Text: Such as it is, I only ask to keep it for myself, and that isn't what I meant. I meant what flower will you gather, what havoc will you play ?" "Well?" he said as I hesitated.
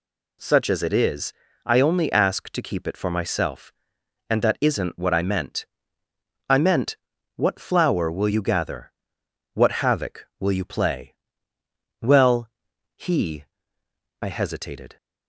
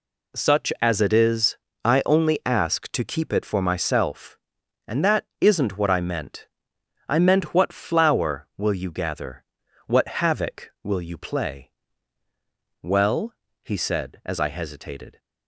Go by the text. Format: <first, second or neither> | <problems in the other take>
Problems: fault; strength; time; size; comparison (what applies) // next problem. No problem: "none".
second | pauses between "meant" and "what"; at 6.9 s; 0.40 s long // skips "said as"; at 13.8 s